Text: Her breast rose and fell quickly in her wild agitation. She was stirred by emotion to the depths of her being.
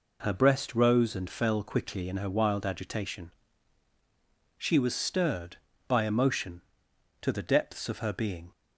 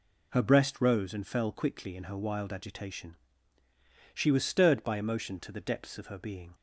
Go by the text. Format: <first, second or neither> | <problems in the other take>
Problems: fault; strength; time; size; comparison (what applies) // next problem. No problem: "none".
neither | none